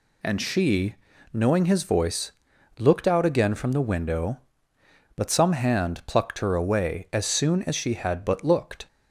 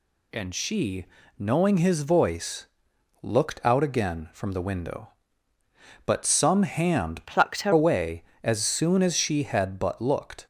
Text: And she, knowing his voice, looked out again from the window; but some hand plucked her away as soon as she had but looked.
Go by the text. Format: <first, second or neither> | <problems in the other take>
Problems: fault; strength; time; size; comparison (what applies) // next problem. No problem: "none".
first | changes voice from "plucked" to "her"; from 7.2 to 7.7 s; 0.5 s long